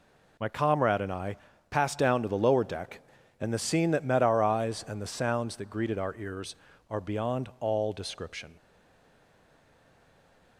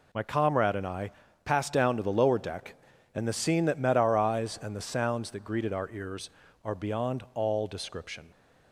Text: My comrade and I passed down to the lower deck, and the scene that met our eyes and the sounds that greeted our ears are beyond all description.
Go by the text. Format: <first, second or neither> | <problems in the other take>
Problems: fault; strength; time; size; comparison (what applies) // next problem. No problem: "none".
second | pauses between "I" and "passed"; slight; at 1.3 s; 0.32 s long; slight in the second // stays silent after the last word; noticeable; from 8.5 s on; 2.0 s long